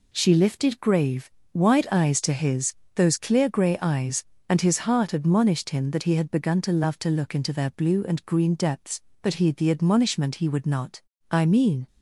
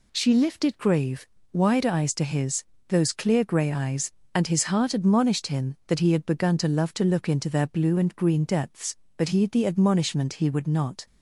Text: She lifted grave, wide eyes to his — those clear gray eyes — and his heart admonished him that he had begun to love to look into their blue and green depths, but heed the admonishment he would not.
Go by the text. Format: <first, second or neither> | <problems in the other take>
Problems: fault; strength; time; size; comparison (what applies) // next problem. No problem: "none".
second | goes on to say "I mean"; from 11.3 s on; 0.56 s long